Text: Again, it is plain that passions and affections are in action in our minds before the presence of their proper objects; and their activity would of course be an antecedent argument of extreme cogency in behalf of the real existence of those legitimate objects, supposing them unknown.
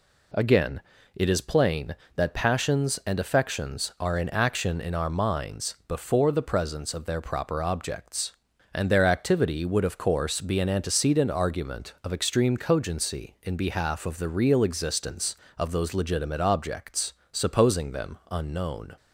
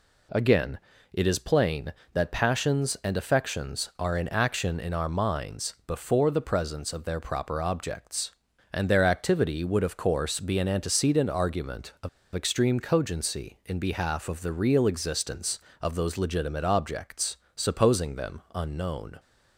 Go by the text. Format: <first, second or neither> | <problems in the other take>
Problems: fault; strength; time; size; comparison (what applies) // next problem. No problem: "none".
first | pauses between "of" and "extreme"; slight; at 12.0 s; 0.26 s long